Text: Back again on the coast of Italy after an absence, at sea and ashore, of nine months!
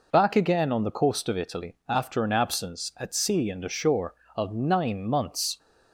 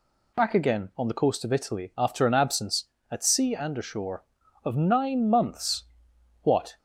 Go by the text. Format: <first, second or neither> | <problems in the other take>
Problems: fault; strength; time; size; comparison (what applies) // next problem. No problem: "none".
first | goes on to say "What"; slight; from 6.4 s on; 0.34 s long